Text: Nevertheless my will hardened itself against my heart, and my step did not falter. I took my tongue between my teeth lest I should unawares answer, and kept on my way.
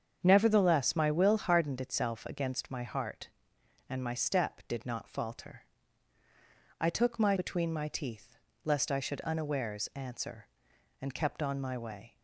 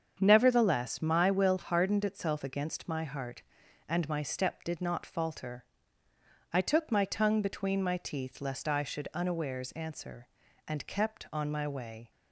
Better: second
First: starts louder than the rest; strong; until 1.2 s; 7.5 dB // skips "tongue"; at 7.3 s // pauses between "teeth" and "lest"; slight; at 8.3 s; 0.30 s long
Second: starts louder than the rest; strong; until 1.2 s; 7.5 dB

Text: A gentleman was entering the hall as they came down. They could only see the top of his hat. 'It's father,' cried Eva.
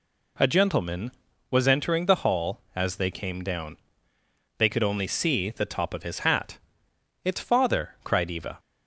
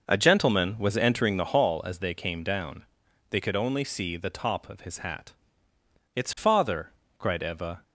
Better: first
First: none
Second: starts louder than the rest; noticeable; until 1.6 s; 6 dB

